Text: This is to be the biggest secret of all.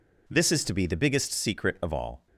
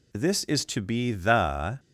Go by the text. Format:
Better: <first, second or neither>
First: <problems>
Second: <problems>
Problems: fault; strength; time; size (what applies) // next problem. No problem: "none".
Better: first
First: none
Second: stops before "biggest secret of all"; at 1.7 s